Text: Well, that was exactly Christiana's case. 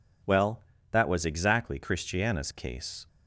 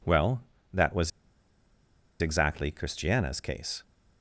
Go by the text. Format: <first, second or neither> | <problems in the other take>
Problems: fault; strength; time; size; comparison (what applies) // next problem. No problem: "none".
first | pauses between "was" and "exactly"; at 1.1 s; 1.1 s long